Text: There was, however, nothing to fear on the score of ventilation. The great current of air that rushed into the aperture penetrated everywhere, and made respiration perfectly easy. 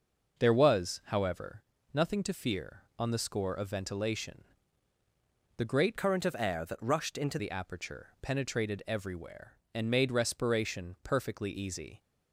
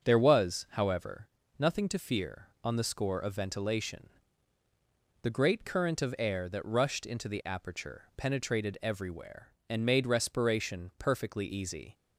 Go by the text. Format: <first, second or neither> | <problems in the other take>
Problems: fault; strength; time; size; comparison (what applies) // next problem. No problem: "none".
second | starts louder than the rest; noticeable; until 1.4 s; 6 dB; also in the second // changes voice from "current" to "into"; from 5.9 to 7.3 s; 1.4 s long